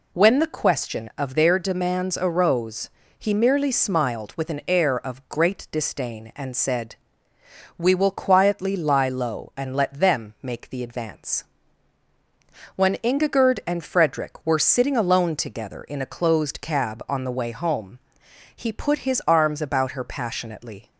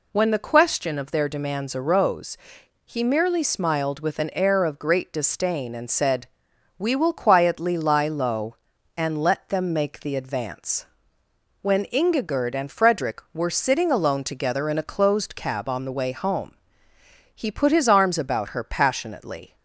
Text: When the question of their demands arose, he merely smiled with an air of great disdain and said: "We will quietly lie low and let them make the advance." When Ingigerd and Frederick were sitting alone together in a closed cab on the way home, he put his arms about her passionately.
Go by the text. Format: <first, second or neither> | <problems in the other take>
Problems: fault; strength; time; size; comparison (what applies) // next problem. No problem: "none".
neither | none